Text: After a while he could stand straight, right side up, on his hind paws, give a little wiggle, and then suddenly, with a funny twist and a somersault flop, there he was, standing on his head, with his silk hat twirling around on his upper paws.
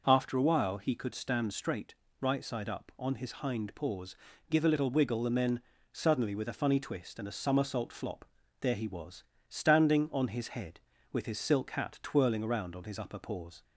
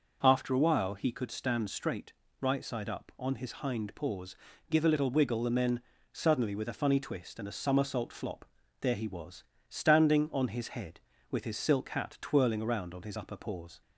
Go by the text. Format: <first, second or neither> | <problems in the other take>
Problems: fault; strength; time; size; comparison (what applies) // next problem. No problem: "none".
neither | pauses between "then" and "suddenly"; slight; the same in both